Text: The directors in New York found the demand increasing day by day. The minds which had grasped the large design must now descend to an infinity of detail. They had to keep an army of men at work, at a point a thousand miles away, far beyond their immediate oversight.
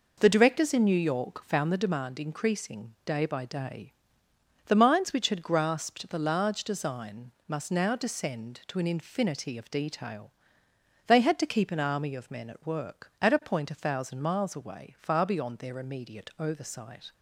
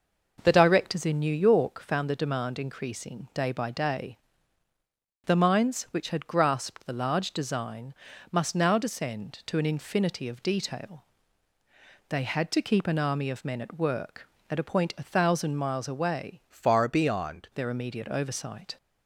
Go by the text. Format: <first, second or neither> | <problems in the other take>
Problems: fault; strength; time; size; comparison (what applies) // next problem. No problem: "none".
first | pauses between "design" and "must"; at 7.9 s; 0.38 s long; slight in the first // changes voice from "far" to "beyond"; from 16.4 to 17.4 s; 1.0 s long